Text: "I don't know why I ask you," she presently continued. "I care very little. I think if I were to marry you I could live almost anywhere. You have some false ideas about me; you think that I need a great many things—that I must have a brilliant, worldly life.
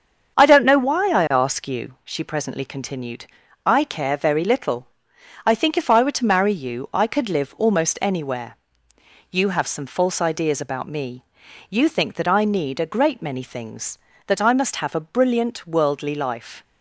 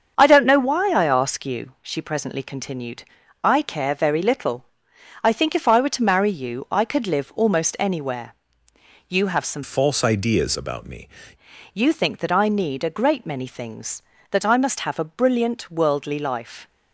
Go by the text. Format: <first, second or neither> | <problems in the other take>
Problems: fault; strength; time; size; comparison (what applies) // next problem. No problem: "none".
first | starts louder than the rest; until 1.1 s; 7 dB; also in the first // changes voice from "false" to "me"; from 9.6 to 11.0 s; 1.4 s long